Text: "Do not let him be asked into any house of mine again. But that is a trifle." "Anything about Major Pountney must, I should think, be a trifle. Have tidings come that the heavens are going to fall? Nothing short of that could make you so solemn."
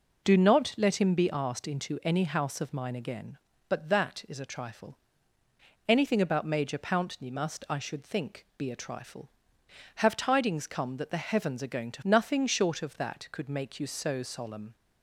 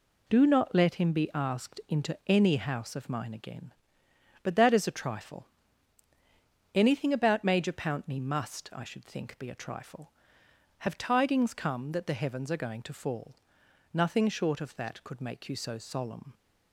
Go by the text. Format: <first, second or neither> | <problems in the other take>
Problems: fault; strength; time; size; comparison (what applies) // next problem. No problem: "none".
second | skips "fall"; at 12.0 s